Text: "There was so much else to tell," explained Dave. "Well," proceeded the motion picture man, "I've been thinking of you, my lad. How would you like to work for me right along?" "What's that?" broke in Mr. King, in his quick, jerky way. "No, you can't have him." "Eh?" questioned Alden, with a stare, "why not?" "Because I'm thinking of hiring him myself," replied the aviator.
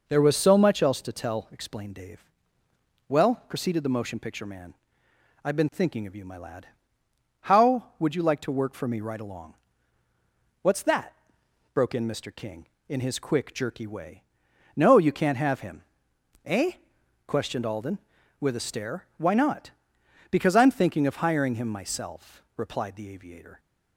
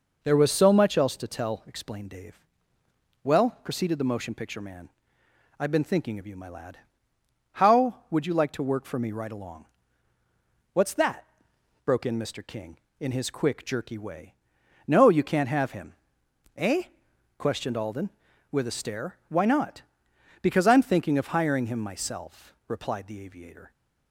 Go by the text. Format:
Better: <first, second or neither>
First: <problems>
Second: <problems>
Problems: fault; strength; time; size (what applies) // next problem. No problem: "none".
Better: neither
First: none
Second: none